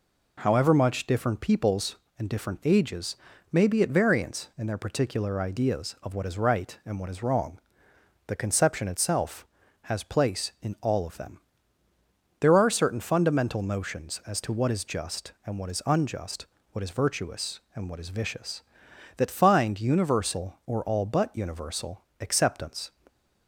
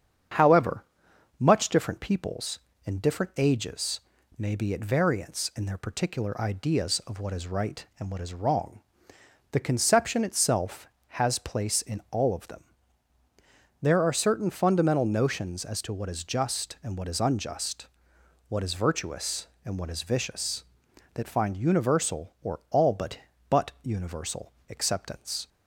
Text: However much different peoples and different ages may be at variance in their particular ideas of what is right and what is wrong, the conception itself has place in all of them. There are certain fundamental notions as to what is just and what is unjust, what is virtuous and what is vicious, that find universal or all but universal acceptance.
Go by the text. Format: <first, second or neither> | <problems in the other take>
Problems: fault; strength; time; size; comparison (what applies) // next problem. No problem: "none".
first | starts louder than the rest; strong; until 1.8 s; 7.5 dB // pauses between "However" and "much"; noticeable; at 0.8 s; 0.54 s long // pauses between "ages" and "may"; at 4.0 s; 0.38 s long; slight in the first // says "but" twice; at 23.5 s // pauses between "universal" and "acceptance"; slight; at 24.5 s; 0.20 s long; slight in the first